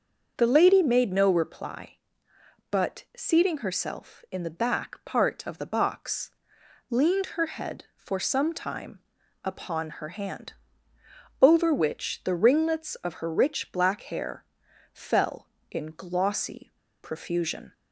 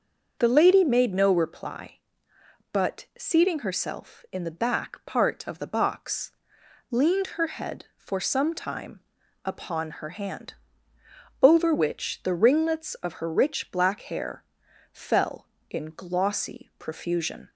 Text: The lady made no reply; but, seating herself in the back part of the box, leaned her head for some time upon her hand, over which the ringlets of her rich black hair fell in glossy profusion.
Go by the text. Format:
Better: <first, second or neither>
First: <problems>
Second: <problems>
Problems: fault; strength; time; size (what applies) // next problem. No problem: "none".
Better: second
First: starts louder than the rest; until 1.4 s; 7 dB // pauses between "time" and "upon"; noticeable; at 8.9 s; 0.46 s long // pauses between "hair" and "fell"; noticeable; at 14.4 s; 0.48 s long // pauses between "glossy" and "profusion"; slight; at 16.7 s; 0.30 s long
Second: starts louder than the rest; until 1.4 s; 6.5 dB // pauses between "time" and "upon"; noticeable; at 8.9 s; 0.46 s long // pauses between "hair" and "fell"; noticeable; at 14.4 s; 0.48 s long